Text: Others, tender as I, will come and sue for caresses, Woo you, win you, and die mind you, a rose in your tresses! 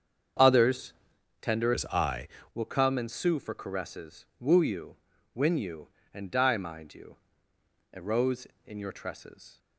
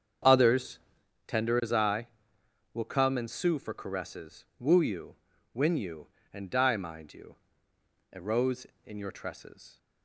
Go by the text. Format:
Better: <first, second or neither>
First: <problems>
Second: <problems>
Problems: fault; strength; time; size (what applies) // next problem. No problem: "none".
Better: second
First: starts louder than the rest; until 1.9 s; 7 dB // changes voice from "as" to "I"; from 1.7 to 2.2 s; 0.5 s long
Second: starts louder than the rest; strong; until 1.7 s; 7.5 dB